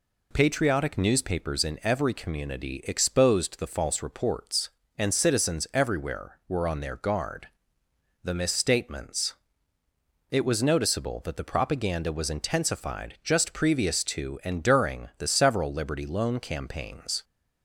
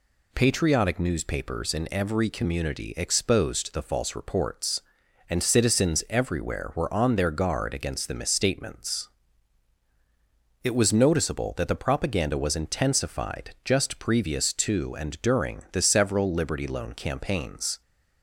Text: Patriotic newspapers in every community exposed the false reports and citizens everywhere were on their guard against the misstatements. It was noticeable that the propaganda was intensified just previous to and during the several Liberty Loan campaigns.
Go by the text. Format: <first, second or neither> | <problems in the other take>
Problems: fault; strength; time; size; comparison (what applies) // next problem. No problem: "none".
second | skips "against"; at 7.8 s